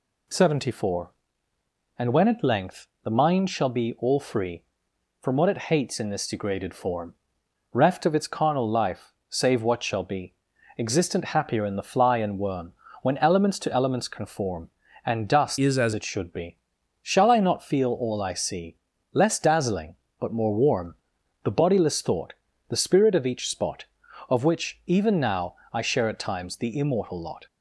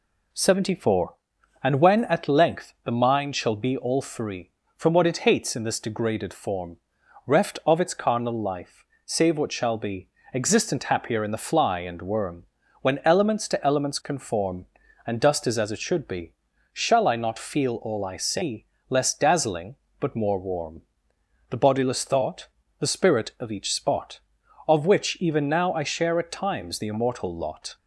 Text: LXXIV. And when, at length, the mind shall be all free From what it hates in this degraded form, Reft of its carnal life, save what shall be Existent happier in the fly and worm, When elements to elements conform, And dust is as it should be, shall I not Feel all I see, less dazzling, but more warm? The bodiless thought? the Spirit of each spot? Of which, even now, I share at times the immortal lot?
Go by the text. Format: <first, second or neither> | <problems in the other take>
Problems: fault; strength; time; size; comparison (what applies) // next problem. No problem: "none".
second | pauses between "be" and "Existent"; noticeable; at 10.3 s; 0.46 s long; slight in the second // changes voice from "is" to "as"; from 15.5 to 15.9 s; 0.4 s long